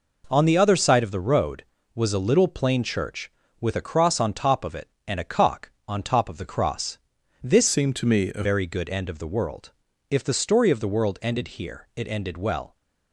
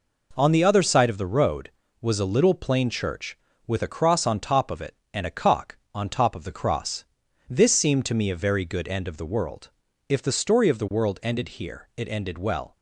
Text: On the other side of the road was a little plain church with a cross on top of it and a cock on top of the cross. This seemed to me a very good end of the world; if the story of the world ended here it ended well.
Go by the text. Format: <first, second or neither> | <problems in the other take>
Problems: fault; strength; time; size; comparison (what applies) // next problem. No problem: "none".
second | changes voice from "seemed" to "a"; from 7.6 to 8.4 s; 0.8 s long